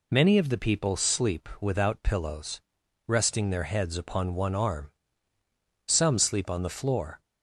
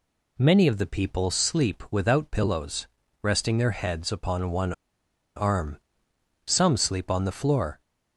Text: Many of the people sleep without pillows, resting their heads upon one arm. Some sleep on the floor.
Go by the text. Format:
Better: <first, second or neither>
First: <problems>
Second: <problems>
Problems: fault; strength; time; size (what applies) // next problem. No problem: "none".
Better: first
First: none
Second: pauses between "one" and "arm"; noticeable; at 4.7 s; 0.64 s long